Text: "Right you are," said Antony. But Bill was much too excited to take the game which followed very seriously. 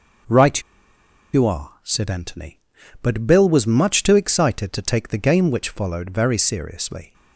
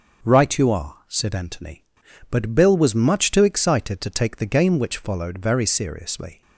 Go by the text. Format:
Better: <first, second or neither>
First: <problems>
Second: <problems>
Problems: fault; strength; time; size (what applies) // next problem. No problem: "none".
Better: second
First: starts louder than the rest; until 2.1 s; 6 dB // pauses between "Right" and "you"; noticeable; at 0.5 s; 0.73 s long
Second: starts louder than the rest; until 1.3 s; 6 dB